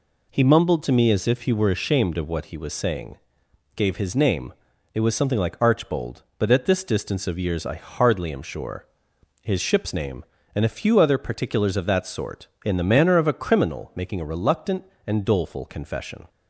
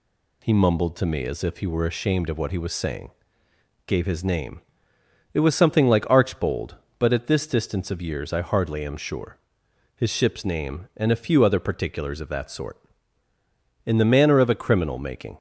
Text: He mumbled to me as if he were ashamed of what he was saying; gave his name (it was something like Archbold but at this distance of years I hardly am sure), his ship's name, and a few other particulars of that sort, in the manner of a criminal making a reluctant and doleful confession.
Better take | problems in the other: first | stops before "a reluctant and doleful confession"; at 15.3 s

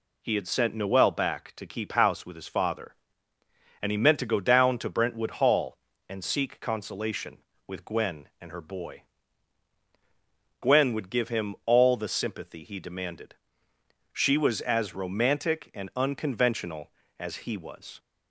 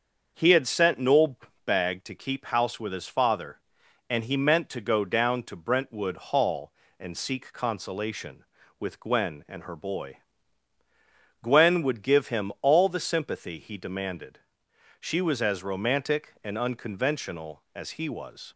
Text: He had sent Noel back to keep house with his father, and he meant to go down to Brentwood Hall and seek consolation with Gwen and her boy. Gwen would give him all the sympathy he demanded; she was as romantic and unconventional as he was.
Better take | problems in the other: first | starts louder than the rest; until 1.3 s; 6.5 dB // says "bag" for "back"; at 1.6 s

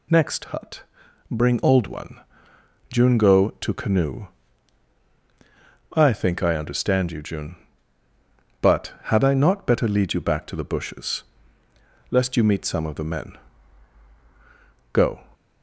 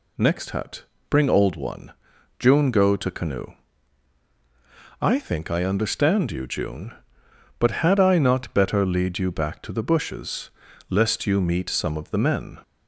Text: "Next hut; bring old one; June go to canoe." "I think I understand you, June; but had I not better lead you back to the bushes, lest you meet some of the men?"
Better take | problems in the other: second | goes on to say "Go"; slight; from 14.9 s on; 0.26 s long

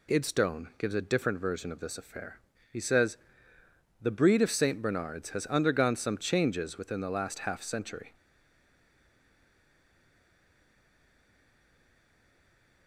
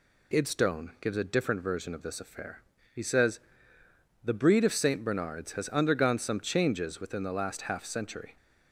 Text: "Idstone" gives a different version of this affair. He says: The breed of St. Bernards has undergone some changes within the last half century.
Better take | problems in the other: second | stays silent after the last word; strong; from 8.1 s on; 4.7 s long

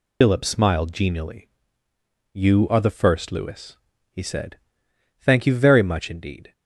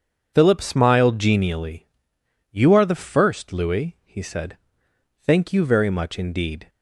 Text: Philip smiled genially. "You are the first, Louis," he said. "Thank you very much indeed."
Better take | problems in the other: second | loses the start of "Philip"; at 0.2 s; 65 ms

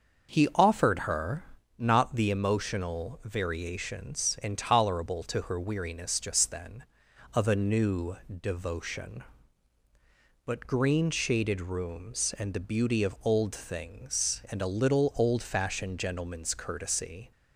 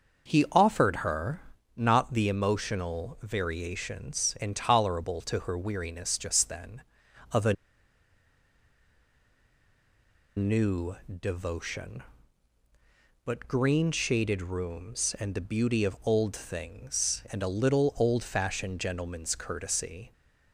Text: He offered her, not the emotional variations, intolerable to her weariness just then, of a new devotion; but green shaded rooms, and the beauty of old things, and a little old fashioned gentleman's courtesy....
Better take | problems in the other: first | starts louder than the rest; until 1.3 s; 6.5 dB; also in the first // pauses between "a" and "new"; strong; at 7.5 s; 2.8 s long

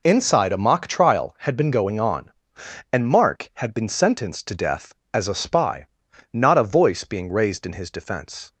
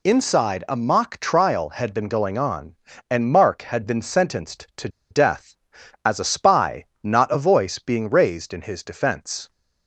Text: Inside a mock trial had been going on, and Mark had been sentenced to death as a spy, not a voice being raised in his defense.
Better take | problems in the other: first | pauses between "to" and "death"; slight; at 4.8 s; 0.22 s long

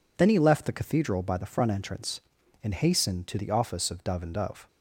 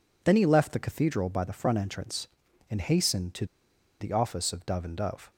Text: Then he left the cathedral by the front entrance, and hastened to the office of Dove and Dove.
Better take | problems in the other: first | pauses between "to" and "the"; noticeable; at 3.4 s; 0.55 s long

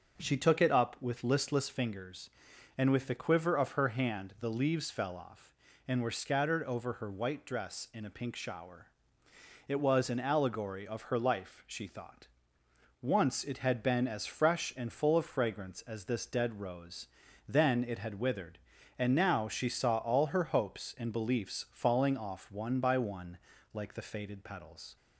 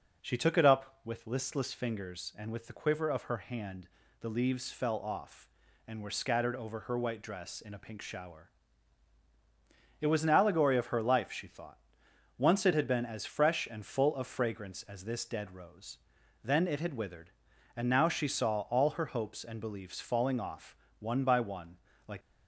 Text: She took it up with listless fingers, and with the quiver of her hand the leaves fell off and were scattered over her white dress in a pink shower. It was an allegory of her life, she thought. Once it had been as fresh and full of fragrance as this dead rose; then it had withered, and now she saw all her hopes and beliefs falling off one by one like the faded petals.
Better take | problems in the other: first | pauses between "hand" and "the"; slight; at 3.8 s; 0.32 s long // pauses between "off" and "one"; slight; at 20.7 s; 0.24 s long // pauses between "one" and "like"; slight; at 21.7 s; 0.28 s long; slight in the first // stops before "the faded petals"; at 22.2 s

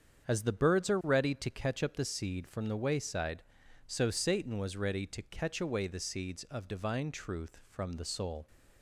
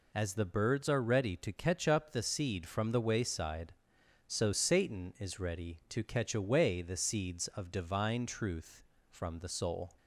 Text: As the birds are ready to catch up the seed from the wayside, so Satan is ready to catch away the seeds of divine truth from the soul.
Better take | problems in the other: second | starts louder than the rest; strong; until 1.3 s; 7.5 dB // says "was" for "is"; at 4.5 s

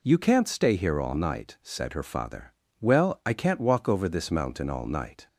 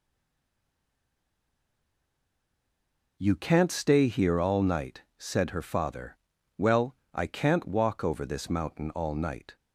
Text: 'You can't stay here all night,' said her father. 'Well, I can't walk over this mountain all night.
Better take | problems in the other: first | stays silent before the first word; strong; until 3.1 s; 3.1 s long

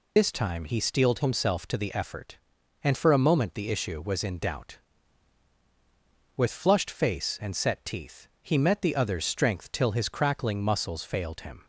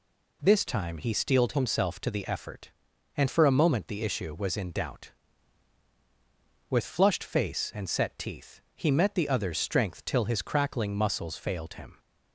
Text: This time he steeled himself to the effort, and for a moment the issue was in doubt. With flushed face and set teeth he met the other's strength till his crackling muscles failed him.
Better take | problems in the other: second | loses the start of "This"; at 0.1 s; 80 ms

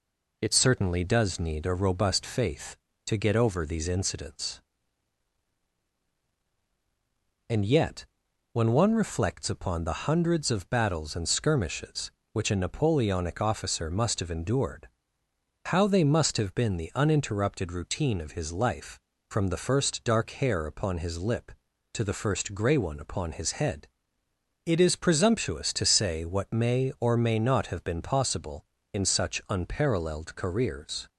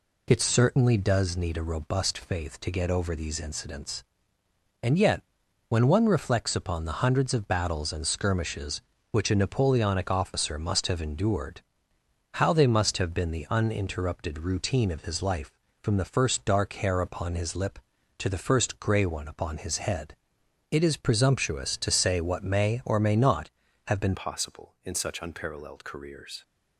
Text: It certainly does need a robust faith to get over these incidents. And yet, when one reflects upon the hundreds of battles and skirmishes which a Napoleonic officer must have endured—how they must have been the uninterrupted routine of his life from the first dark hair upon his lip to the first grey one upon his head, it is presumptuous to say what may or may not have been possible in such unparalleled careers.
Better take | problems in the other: first | changes voice at "possible"; from 24.1 s on; 2.3 s long

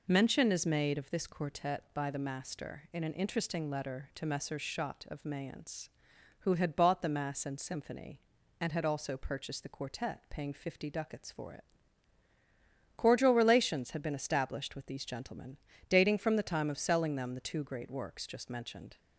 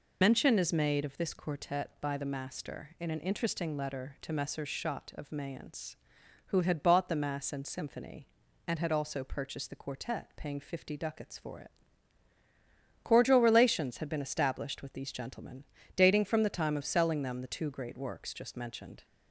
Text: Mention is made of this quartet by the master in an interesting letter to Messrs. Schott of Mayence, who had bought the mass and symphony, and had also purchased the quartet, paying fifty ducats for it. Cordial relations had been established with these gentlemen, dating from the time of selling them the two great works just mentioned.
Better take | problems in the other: first | loses the start of "Mention"; at 0.2 s; 65 ms

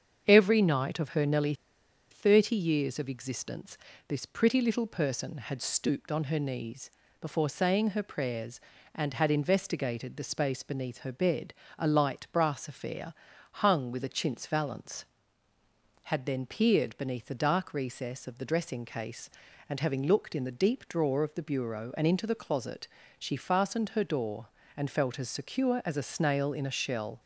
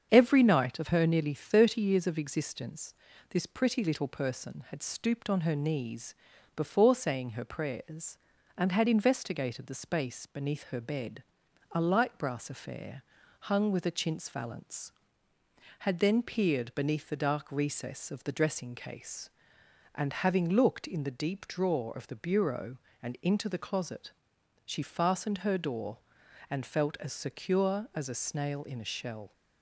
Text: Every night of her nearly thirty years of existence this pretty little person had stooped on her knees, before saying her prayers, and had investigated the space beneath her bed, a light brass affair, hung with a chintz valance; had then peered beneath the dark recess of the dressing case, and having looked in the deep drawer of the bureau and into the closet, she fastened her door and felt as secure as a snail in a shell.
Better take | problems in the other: second | starts louder than the rest; strong; until 1.2 s; 7.5 dB; strong in the second // pauses between "nearly" and "thirty"; noticeable; at 1.5 s; 0.58 s long // pauses between "existence" and "this"; slight; at 3.7 s; 0.32 s long; slight in the second

